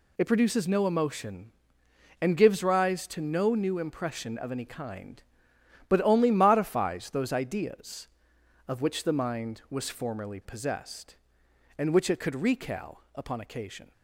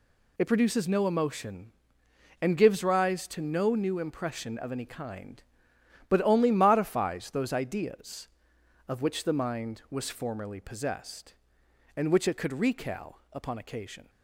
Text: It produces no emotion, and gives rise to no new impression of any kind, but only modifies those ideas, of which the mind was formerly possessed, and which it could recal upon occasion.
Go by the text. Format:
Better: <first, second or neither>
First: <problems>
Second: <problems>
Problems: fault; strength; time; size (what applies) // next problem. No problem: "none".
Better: neither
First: none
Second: none